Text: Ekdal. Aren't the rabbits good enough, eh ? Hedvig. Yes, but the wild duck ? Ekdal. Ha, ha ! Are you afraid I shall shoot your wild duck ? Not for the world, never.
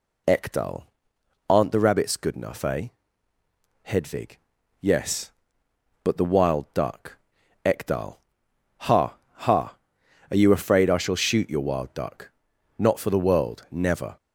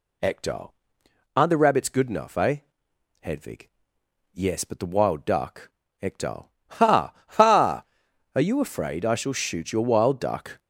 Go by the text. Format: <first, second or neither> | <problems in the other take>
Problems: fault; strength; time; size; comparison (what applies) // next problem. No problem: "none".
first | stops before "Not for the world never"; at 10.5 s